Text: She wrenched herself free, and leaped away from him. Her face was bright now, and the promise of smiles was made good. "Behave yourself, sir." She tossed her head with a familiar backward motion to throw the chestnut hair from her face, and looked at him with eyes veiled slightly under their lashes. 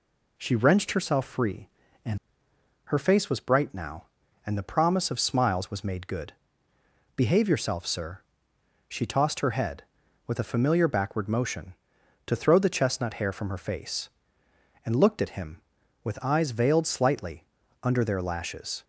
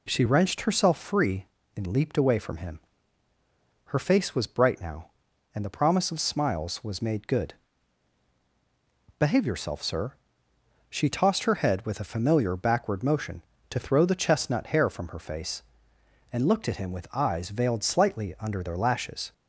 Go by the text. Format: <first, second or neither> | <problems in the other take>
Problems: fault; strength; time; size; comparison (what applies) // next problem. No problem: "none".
second | skips "leaped away from him"; at 2.5 s // pauses between "slightly" and "under"; at 17.4 s; 0.40 s long